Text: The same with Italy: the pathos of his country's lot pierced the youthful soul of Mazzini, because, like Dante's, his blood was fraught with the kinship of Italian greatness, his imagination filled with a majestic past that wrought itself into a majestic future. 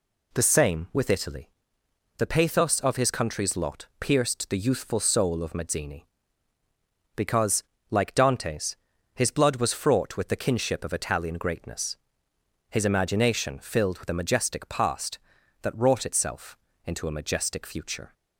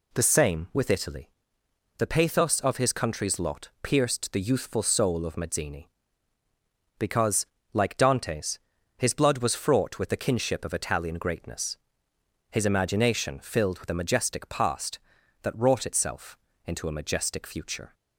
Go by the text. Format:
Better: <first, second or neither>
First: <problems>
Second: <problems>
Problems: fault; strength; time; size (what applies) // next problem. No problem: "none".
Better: neither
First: pauses between "itself" and "into"; slight; at 16.5 s; 0.30 s long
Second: pauses between "itself" and "into"; slight; at 16.3 s; 0.30 s long